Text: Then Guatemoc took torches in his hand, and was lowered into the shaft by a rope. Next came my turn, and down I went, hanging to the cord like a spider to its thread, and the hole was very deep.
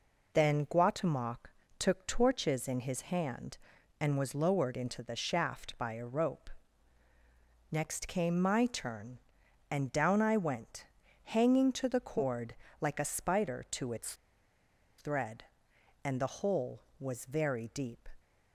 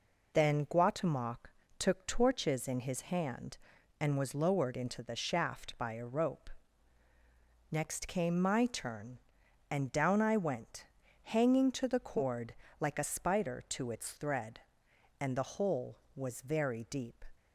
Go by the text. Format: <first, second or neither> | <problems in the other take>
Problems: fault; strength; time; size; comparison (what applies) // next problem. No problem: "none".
second | pauses between "Guatemoc" and "took"; slight; at 1.4 s; 0.30 s long; slight in the second // pauses between "cord" and "like"; slight; at 12.5 s; 0.26 s long; slight in the second // pauses between "its" and "thread"; noticeable; at 14.1 s; 0.84 s long